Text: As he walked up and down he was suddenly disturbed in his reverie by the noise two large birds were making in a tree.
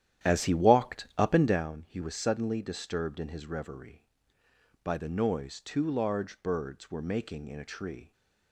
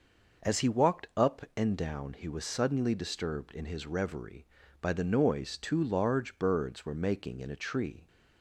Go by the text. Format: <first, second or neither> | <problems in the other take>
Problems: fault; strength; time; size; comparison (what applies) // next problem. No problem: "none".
second | starts louder than the rest; strong; until 1.6 s; 11 dB